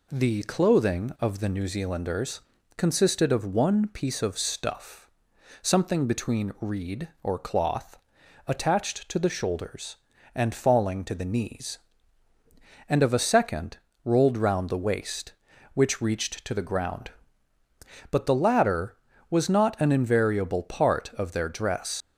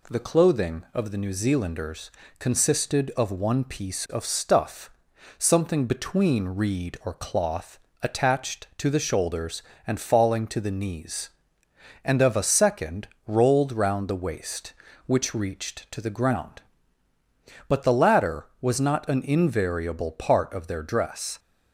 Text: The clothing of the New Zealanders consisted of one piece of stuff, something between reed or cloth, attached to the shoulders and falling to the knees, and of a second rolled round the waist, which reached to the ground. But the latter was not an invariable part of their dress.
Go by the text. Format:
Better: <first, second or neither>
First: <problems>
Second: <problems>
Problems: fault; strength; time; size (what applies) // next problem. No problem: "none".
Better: second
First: pauses between "Zealanders" and "consisted"; slight; at 2.4 s; 0.34 s long // pauses between "second" and "rolled"; slight; at 13.7 s; 0.26 s long // leaves "dress" unfinished; at 22.0 s; 85 ms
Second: pauses between "Zealanders" and "consisted"; slight; at 2.0 s; 0.28 s long // pauses between "second" and "rolled"; slight; at 13.0 s; 0.18 s long